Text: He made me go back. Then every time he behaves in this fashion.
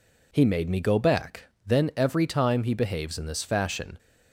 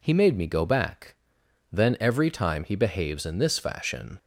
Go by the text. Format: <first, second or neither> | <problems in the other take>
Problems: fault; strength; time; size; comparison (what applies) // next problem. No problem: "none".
neither | none